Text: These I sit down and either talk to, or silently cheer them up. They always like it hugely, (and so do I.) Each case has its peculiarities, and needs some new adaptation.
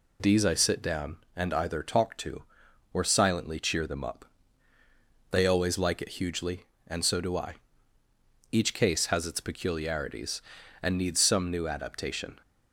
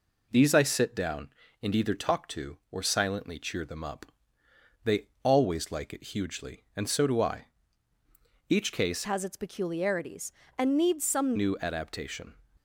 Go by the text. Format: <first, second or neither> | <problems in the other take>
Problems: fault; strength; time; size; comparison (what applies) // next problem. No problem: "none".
first | changes voice from "has" to "some"; from 9.0 to 11.3 s; 2.3 s long